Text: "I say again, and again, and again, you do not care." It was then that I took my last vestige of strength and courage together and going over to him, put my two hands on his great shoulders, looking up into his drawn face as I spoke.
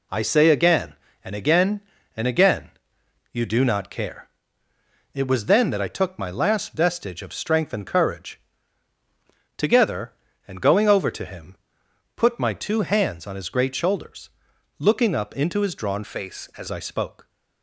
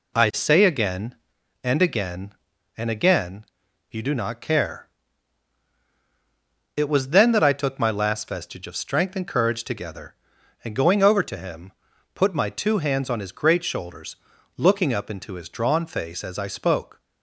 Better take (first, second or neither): second